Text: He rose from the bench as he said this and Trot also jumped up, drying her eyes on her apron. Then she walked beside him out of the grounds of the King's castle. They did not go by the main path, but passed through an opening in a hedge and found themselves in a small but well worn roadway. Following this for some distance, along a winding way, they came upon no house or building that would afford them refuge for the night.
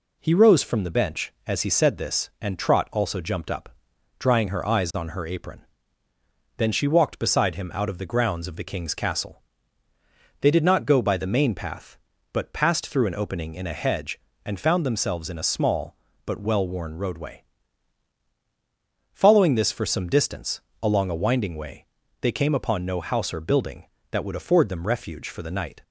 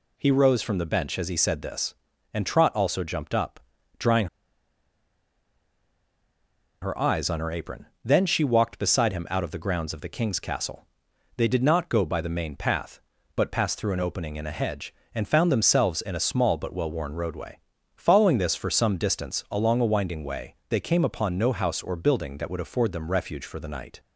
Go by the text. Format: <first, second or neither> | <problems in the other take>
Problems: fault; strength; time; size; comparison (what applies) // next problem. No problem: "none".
first | pauses between "drying" and "her"; strong; at 4.2 s; 2.5 s long